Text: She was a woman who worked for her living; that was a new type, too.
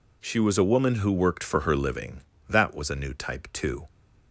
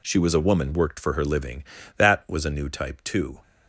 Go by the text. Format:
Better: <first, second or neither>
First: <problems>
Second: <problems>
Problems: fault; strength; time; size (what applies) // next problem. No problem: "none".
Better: first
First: none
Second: skips "who"; at 0.7 s